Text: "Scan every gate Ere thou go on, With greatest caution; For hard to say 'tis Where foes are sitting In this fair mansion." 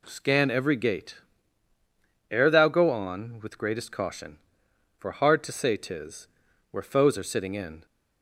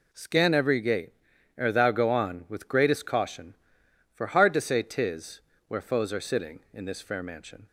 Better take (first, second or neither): second